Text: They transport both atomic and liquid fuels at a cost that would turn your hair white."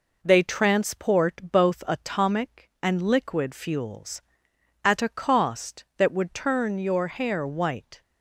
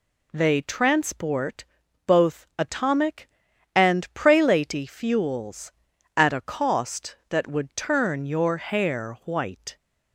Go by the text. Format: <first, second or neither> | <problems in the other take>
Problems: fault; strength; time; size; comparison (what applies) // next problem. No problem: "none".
first | pauses between "transport" and "both"; at 1.6 s; 0.42 s long // says "prelaty" for "liquid"; at 4.1 s